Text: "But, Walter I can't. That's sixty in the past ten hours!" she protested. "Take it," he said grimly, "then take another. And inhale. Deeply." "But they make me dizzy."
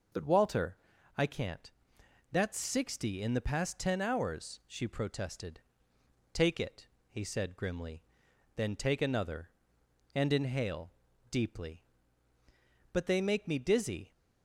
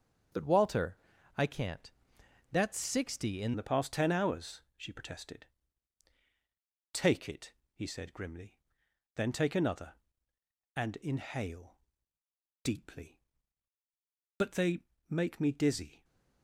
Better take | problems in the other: first | starts louder than the rest; until 1.7 s; 7 dB // pauses between "Walter" and "I"; at 0.9 s; 0.40 s long; also in the first // changes voice at "the"; from 3.5 s on; 12.5 s long // pauses between "they" and "make"; slight; at 14.7 s; 0.32 s long

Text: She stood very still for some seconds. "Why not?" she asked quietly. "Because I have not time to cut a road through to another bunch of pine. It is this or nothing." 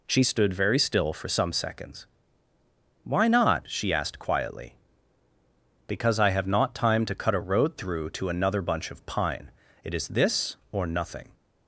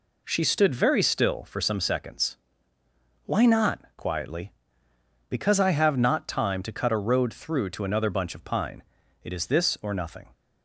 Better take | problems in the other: first | skips "she asked"; at 3.9 s

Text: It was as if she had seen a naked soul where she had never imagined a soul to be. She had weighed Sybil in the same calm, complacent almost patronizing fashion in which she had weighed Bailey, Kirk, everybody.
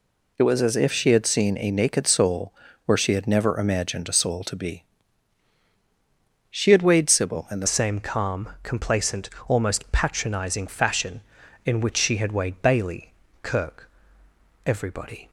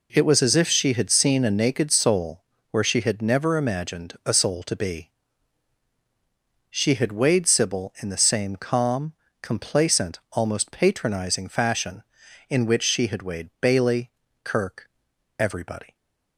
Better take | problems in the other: second | pauses between "soul" and "where"; slight; at 2.5 s; 0.32 s long; slight in the second // changes voice at "same"; from 7.6 s on; 7.6 s long // pauses between "complacent" and "almost"; slight; at 9.2 s; 0.18 s long

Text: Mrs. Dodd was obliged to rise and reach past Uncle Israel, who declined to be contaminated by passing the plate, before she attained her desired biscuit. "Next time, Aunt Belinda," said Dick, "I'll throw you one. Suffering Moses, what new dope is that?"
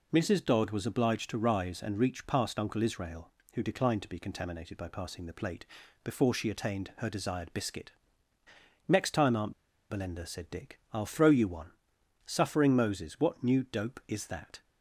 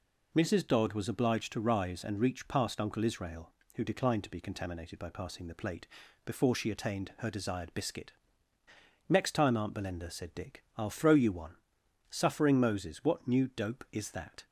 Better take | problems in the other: second | pauses between "Aunt" and "Belinda"; at 9.5 s; 0.37 s long

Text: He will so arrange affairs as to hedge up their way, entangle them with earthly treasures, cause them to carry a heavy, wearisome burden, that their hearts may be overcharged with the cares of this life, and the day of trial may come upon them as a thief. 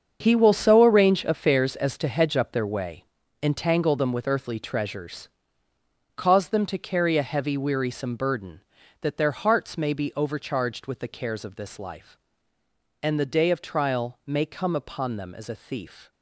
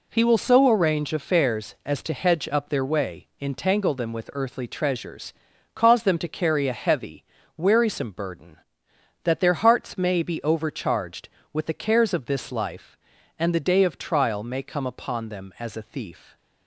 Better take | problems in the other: second | gets quieter; strong; throughout; 12 dB

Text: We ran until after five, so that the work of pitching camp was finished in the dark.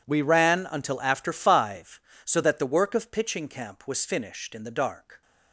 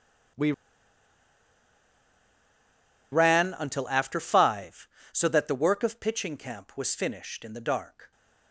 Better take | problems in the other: first | pauses between "We" and "ran"; strong; at 0.5 s; 2.6 s long

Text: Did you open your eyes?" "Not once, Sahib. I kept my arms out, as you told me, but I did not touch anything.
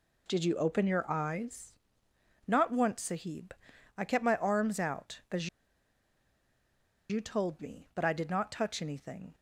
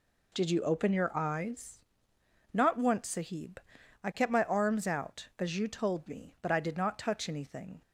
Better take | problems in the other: second | pauses between "as" and "you"; strong; at 5.4 s; 1.6 s long

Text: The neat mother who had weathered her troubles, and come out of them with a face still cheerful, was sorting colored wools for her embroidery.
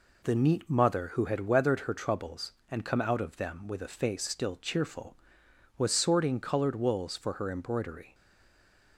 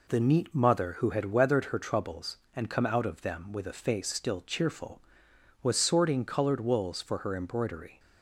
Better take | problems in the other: second | stays silent after the last word; slight; from 8.1 s on; 0.8 s long

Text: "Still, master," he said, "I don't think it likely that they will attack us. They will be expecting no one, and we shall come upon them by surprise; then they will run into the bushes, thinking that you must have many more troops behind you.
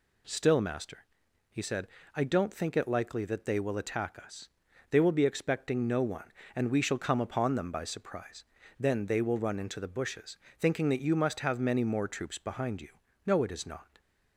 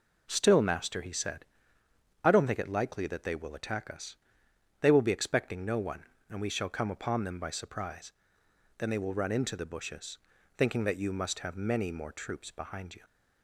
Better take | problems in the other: second | goes on to say "No it is not"; noticeable; from 13.2 s on; 0.76 s long

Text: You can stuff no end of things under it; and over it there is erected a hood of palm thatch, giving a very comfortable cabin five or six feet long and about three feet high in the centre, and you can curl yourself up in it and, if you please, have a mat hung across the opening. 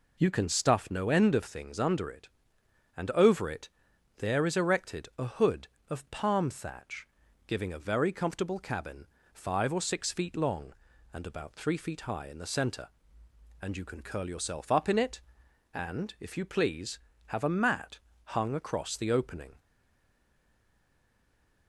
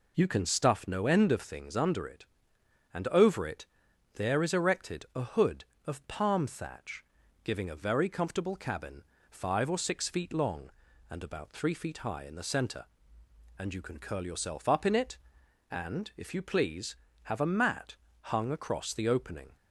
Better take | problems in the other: second | pauses between "it" and "there"; noticeable; at 3.6 s; 0.48 s long; noticeable in the second // pauses between "cabin" and "five"; slight; at 9.0 s; 0.26 s long; slight in the second // pauses between "mat" and "hung"; slight; at 17.9 s; 0.30 s long; slight in the second // stays silent after the last word; noticeable; from 19.5 s on; 2.1 s long

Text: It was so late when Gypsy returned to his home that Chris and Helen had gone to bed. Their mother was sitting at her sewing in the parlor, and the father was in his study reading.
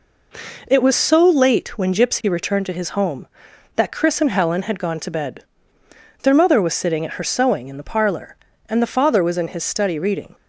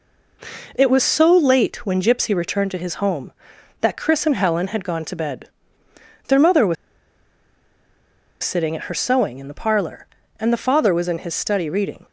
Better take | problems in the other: first | pauses between "was" and "sitting"; strong; at 6.7 s; 1.6 s long

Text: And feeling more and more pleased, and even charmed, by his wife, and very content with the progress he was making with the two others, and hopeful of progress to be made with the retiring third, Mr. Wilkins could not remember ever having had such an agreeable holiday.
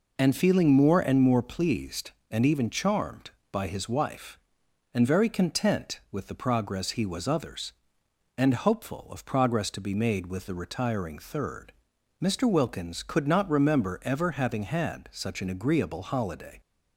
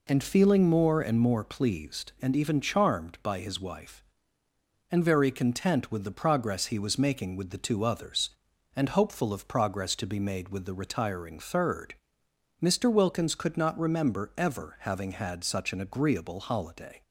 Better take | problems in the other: second | skips "making with the two"; at 7.2 s

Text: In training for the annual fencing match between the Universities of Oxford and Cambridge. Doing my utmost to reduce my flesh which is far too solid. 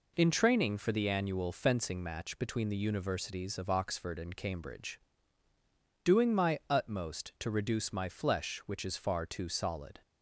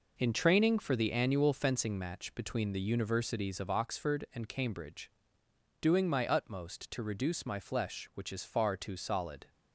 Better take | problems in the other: first | gets quieter; strong; throughout; 8 dB

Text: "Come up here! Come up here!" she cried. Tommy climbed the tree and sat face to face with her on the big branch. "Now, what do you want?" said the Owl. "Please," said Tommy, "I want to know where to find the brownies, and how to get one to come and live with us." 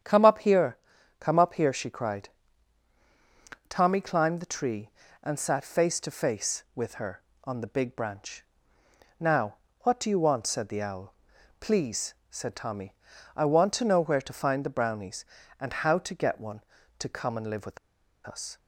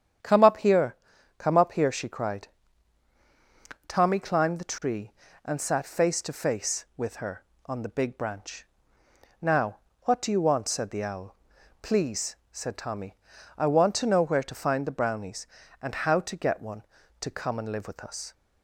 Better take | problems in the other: second | starts louder than the rest; strong; until 1.4 s; 8.5 dB; strong in the second // pauses between "with" and "us"; noticeable; at 17.7 s; 0.48 s long

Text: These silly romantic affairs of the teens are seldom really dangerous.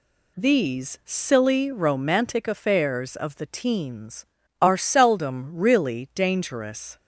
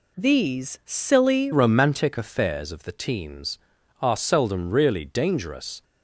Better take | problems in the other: first | changes voice at "romantic"; from 1.5 s on; 4.3 s long

